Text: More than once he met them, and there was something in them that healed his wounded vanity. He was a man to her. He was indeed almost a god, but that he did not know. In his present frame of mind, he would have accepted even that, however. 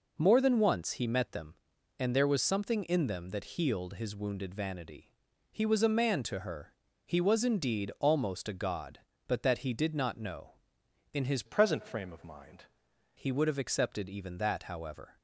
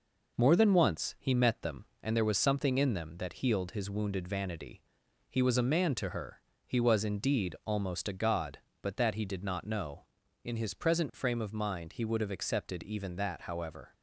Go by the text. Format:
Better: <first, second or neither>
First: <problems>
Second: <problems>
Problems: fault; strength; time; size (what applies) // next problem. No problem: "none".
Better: second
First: changes voice from "present" to "mind"; from 11.4 to 12.6 s; 1.2 s long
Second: none